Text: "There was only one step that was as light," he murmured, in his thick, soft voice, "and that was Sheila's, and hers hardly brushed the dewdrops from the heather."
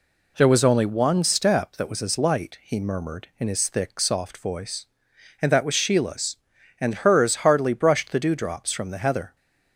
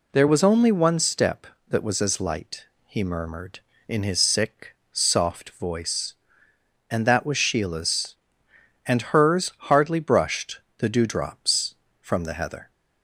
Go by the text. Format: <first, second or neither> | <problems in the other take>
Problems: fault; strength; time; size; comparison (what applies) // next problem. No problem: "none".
first | says "sick" for "thick"; at 4.1 s // pauses between "brushed" and "the"; slight; at 10.6 s; 0.16 s long